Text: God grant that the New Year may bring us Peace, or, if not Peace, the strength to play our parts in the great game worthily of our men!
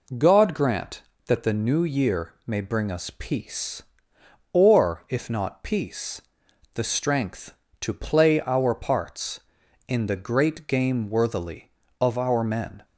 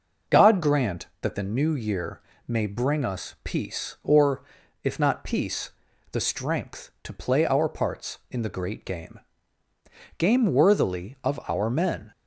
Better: first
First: none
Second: pauses between "Year" and "may"; slight; at 2.2 s; 0.26 s long // says "game" twice; at 10.1 s

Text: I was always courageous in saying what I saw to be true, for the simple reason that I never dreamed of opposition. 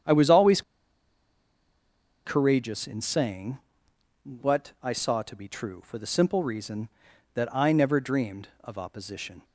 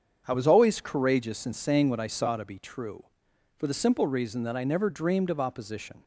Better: second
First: starts louder than the rest; strong; until 2.6 s; 8.5 dB // pauses between "always" and "courageous"; strong; at 0.6 s; 1.6 s long // pauses between "saying" and "what"; noticeable; at 3.5 s; 0.66 s long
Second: starts louder than the rest; until 1.2 s; 7 dB

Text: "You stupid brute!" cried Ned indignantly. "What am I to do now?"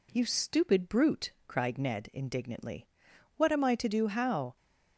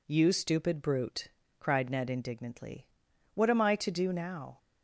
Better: second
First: says "how" for "now"; at 4.0 s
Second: none

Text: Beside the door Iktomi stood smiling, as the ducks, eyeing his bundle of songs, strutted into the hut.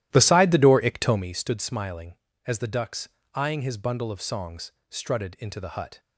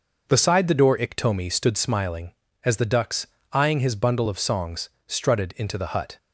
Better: second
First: starts louder than the rest; strong; until 1.3 s; 13.5 dB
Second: none

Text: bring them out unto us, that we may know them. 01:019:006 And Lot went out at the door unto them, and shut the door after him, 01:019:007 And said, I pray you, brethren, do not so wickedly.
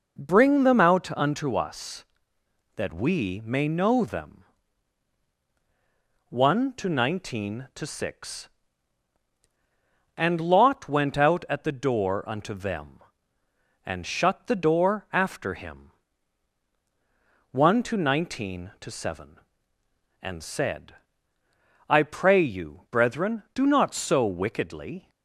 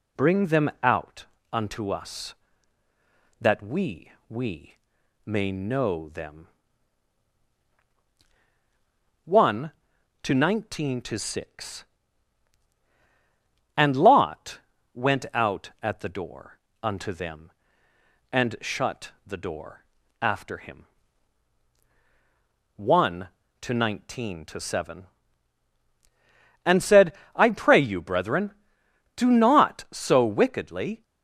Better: first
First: none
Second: pauses between "out" and "unto"; slight; at 1.2 s; 0.26 s long // says "we" twice; at 4.2 s // pauses between "Lot" and "went"; slight; at 14.5 s; 0.36 s long // pauses between "door" and "unto"; slight; at 16.5 s; 0.26 s long // pauses between "door" and "after"; slight; at 19.8 s; 0.36 s long

